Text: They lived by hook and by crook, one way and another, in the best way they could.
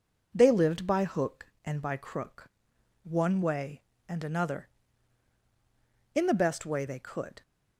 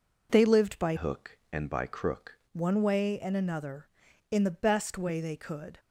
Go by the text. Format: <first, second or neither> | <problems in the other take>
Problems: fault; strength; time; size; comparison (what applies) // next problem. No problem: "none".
first | changes voice from "hook" to "crook"; from 0.9 to 2.3 s; 1.4 s long